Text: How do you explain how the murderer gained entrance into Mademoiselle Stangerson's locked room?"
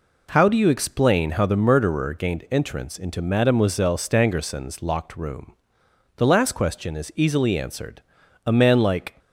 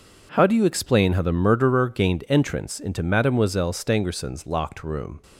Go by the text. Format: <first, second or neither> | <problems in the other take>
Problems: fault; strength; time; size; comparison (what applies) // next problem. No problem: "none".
second | goes on to say "The last question is easily answered A man like"; strong; from 6.1 s on; 2.9 s long